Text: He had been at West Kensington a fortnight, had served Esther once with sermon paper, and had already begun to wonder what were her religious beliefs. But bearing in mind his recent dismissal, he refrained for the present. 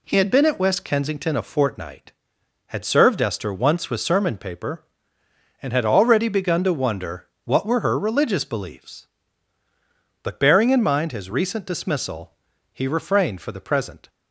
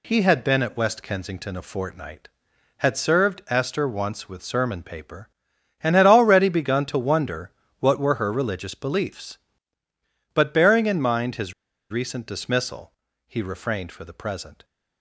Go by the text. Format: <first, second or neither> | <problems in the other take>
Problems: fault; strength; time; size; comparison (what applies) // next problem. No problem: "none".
first | pauses between "wonder" and "what"; slight; at 7.4 s; 0.30 s long; slight in the first // pauses between "his" and "recent"; at 11.5 s; 0.39 s long